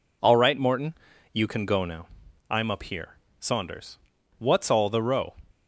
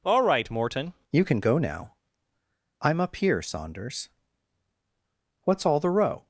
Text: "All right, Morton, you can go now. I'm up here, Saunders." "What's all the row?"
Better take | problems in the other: first | changes voice at "you"; from 1.1 s on; 5.1 s long

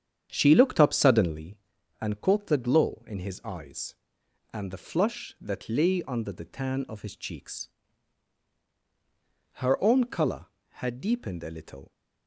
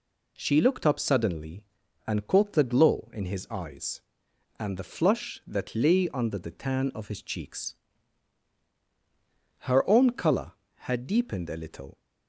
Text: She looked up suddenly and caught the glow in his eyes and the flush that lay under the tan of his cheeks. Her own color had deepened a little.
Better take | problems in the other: second | starts louder than the rest; strong; until 1.5 s; 8.5 dB

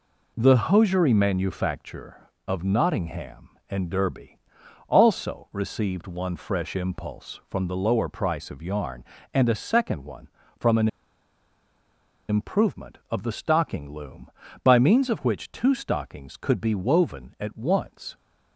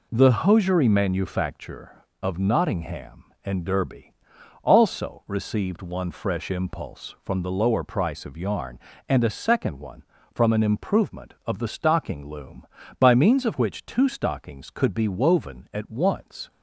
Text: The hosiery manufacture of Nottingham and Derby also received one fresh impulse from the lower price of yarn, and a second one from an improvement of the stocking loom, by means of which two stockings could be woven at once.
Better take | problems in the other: second | pauses between "Derby" and "also"; noticeable; at 4.3 s; 0.48 s long; noticeable in the second // pauses between "an" and "improvement"; strong; at 10.8 s; 1.4 s long

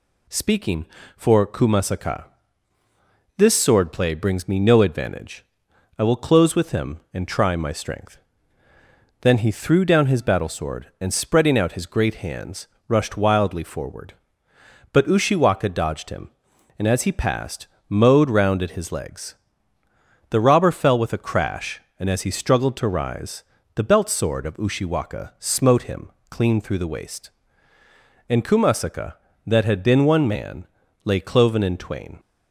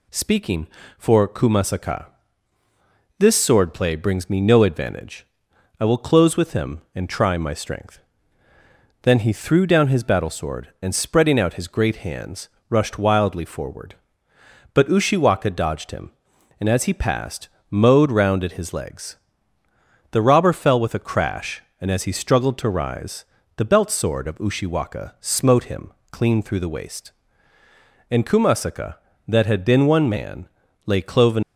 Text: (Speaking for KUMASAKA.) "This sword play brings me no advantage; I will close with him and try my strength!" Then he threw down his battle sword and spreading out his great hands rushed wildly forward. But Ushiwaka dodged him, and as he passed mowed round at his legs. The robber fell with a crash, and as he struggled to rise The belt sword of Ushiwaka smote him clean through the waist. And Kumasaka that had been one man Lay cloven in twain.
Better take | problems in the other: first | pauses between "hands" and "rushed"; slight; at 12.4 s; 0.22 s long; slight in the first // pauses between "passed" and "mowed"; slight; at 17.4 s; 0.20 s long; slight in the first // pauses between "rise" and "The"; slight; at 23.2 s; 0.32 s long; slight in the first // pauses between "him" and "clean"; slight; at 25.9 s; 0.20 s long; slight in the first // pauses between "man" and "Lay"; at 30.4 s; 0.38 s long; also in the first // stops before "in twain"; at 31.4 s

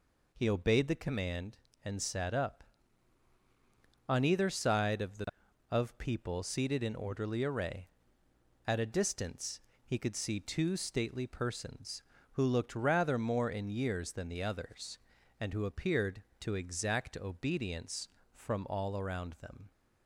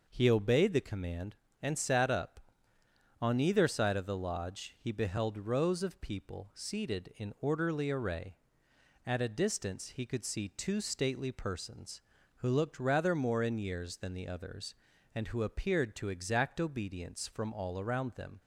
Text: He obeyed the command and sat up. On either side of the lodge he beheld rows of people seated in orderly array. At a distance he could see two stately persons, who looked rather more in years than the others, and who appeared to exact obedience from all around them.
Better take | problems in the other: second | skips "lodge he beheld rows"; at 5.4 s // pauses between "distance" and "he"; slight; at 9.6 s; 0.24 s long

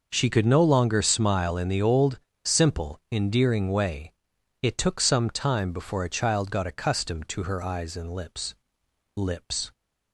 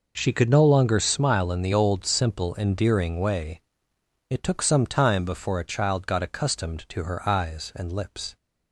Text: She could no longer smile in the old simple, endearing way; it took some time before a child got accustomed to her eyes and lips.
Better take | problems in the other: second | pauses between "old" and "simple"; slight; at 2.1 s; 0.26 s long // says "lips" twice; at 9.1 s

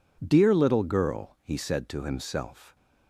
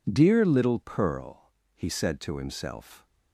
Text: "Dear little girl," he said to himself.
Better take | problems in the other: first | says "pearl" for "girl"; at 0.7 s

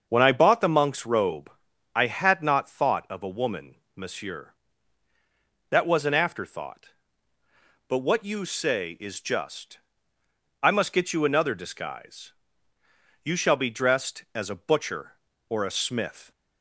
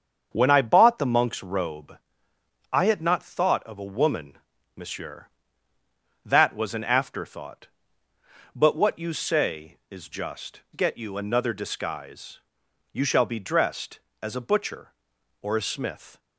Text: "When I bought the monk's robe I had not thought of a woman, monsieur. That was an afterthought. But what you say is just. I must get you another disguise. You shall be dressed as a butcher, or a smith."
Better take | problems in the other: first | starts louder than the rest; strong; until 1.3 s; 7.5 dB; also in the first // pauses between "robe" and "I"; noticeable; at 1.9 s; 0.74 s long; also in the first // skips "I must"; at 10.6 s

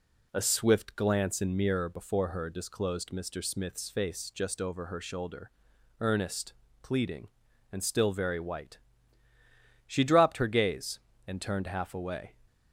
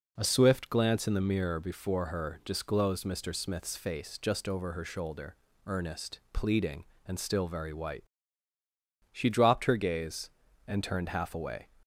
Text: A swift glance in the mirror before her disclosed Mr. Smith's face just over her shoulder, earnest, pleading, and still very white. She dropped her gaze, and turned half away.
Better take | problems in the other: second | skips "the"; at 1.5 s

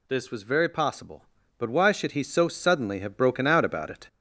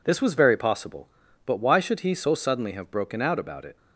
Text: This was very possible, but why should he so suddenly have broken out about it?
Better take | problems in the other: second | gets louder; throughout; 4 dB

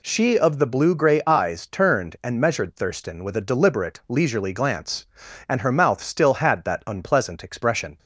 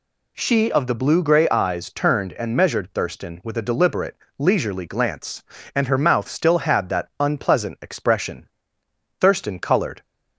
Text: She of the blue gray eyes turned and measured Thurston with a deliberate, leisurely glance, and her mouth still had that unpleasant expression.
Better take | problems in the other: first | goes on to say "Thurston colored"; noticeable; from 9.1 s on; 0.84 s long

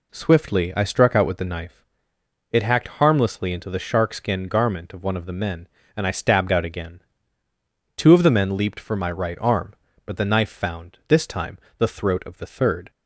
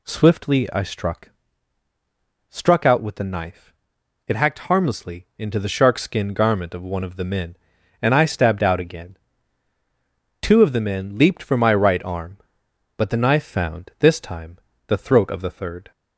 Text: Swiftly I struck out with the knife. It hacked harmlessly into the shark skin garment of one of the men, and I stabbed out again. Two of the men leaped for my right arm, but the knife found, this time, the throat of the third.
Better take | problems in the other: first | says "struck" twice; at 2.4 s

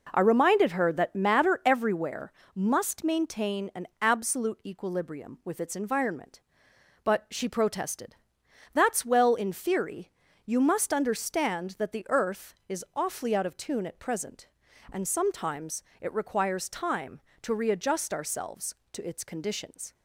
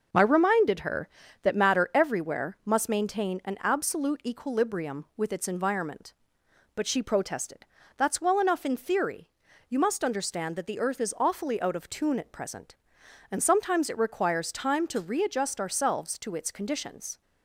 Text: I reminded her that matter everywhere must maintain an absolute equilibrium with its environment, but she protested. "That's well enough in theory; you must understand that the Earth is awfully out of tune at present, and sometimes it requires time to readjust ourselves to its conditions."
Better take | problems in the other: second | pauses between "everywhere" and "must"; slight; at 2.3 s; 0.24 s long // skips "enough"; at 9.3 s // pauses between "sometimes" and "it"; slight; at 15.8 s; 0.16 s long

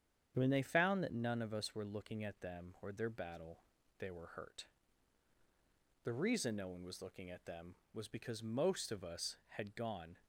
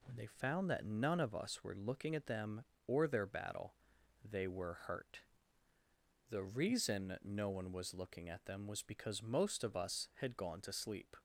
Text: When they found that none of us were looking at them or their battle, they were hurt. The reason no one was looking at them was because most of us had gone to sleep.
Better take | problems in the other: second | starts louder than the rest; strong; until 1.3 s; 8 dB // stops before "to sleep"; at 10.2 s

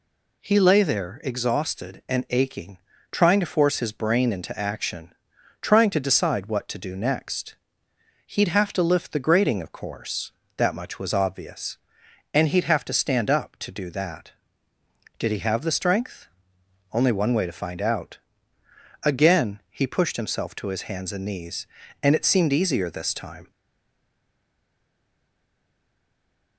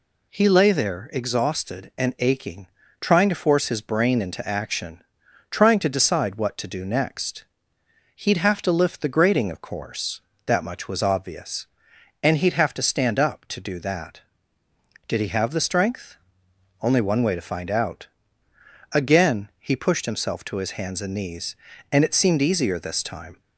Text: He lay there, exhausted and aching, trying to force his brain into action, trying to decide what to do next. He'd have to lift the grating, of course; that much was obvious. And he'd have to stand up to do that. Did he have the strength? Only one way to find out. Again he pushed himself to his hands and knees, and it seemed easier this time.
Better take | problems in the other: second | stays silent after the last word; strong; from 23.5 s on; 3.0 s long

